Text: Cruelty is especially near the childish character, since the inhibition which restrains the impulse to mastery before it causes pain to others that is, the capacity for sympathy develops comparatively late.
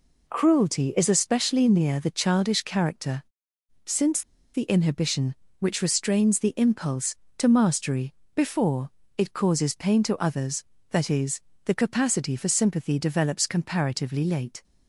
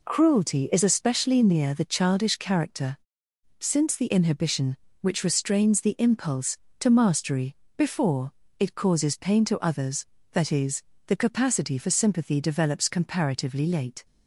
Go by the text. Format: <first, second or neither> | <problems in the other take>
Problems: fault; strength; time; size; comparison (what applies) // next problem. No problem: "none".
second | pauses between "since" and "the"; slight; at 4.2 s; 0.33 s long // pauses between "mastery" and "before"; slight; at 8.1 s; 0.18 s long; slight in the second // pauses between "before" and "it"; slight; at 8.8 s; 0.28 s long; slight in the second